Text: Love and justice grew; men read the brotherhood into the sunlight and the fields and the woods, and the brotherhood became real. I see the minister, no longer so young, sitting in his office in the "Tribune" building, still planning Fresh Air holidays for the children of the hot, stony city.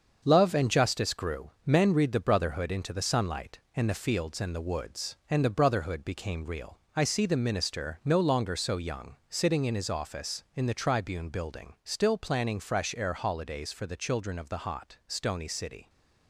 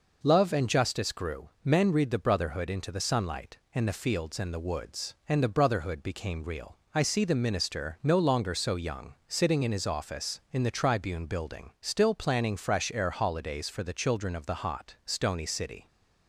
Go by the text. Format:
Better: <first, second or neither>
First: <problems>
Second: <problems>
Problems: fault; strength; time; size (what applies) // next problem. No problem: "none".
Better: second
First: gets quieter; throughout; 6.5 dB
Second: none